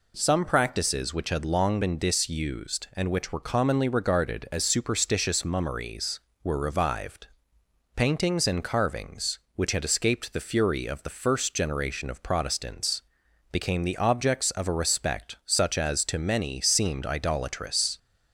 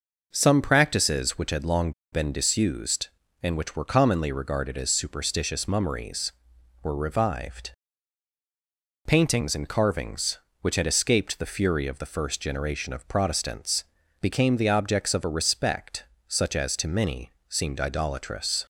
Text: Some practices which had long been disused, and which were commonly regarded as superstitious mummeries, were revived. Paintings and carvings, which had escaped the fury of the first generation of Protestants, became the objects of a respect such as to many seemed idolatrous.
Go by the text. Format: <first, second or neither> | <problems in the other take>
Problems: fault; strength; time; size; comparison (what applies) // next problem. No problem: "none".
first | pauses between "long" and "been"; slight; at 1.9 s; 0.21 s long // pauses between "respect" and "such"; slight; at 16.0 s; 0.22 s long // pauses between "many" and "seemed"; slight; at 17.3 s; 0.16 s long